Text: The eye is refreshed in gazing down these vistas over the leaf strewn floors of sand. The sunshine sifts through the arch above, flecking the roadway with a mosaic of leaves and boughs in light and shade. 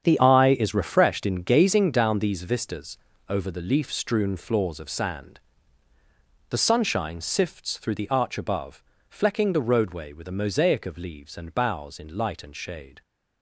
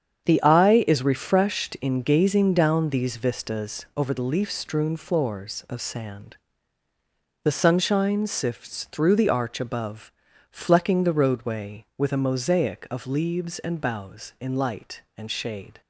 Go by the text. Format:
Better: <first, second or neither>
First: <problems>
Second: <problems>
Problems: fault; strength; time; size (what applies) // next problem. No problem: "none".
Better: second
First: starts louder than the rest; strong; until 1.0 s; 8 dB // changes voice at "eye"; from 0.1 s on; 12.9 s long // pauses between "vistas" and "over"; slight; at 2.9 s; 0.28 s long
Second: starts louder than the rest; strong; until 1.3 s; 8 dB